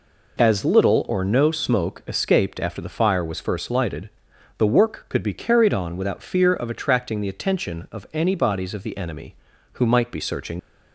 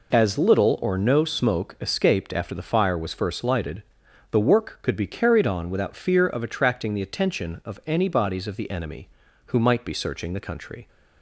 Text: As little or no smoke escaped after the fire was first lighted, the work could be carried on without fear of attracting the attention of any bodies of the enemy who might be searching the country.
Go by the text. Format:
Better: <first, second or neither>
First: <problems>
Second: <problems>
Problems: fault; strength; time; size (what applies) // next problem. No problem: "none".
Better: second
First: stops before "the country"; at 10.5 s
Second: none